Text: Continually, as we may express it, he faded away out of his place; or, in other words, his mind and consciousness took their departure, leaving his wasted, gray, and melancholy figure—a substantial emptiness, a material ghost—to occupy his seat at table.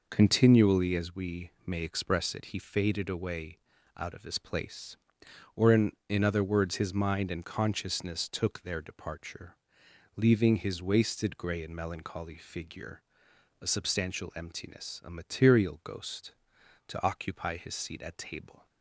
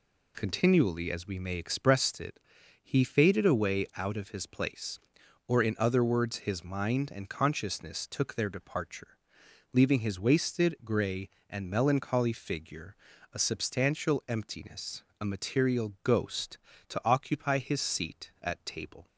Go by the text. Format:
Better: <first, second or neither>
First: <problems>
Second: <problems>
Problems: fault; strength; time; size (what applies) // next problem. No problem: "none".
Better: second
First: pauses between "we" and "may"; slight; at 1.5 s; 0.16 s long // pauses between "away" and "out"; slight; at 3.5 s; 0.36 s long // says "in" twice; at 6.0 s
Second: none